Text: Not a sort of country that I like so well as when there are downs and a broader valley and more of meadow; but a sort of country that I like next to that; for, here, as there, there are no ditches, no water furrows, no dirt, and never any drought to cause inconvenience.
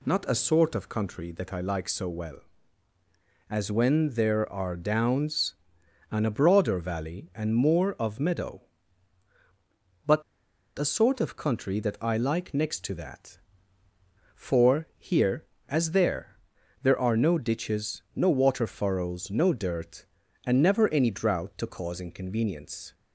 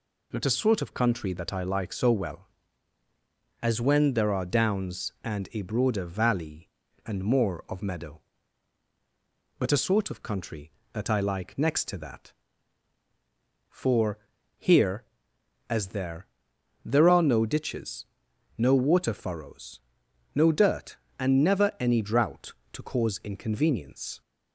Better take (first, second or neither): second